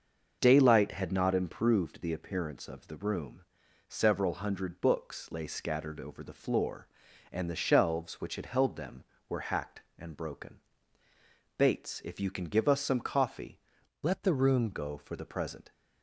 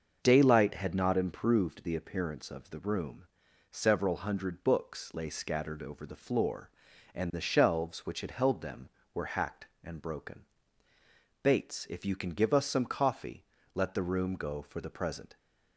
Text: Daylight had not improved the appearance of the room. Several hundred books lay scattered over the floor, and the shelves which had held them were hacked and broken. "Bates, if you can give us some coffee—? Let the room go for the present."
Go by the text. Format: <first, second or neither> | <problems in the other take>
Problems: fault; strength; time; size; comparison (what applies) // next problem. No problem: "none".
second | starts louder than the rest; until 1.4 s; 6 dB; also in the second // changes voice from "Let" to "room"; from 14.0 to 14.6 s; 0.6 s long